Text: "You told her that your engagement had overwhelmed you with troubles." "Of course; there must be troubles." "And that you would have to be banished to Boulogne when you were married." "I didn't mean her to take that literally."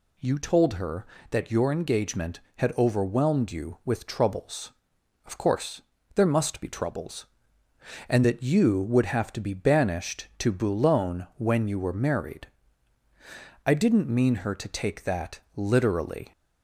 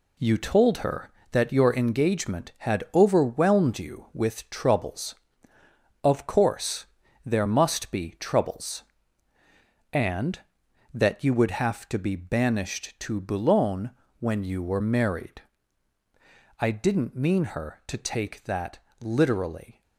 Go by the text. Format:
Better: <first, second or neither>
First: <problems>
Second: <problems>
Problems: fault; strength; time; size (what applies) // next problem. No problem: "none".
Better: first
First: none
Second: gets quieter; throughout; 6.5 dB // pauses between "Boulogne" and "when"; slight; at 13.9 s; 0.28 s long // pauses between "that" and "literally"; slight; at 18.7 s; 0.24 s long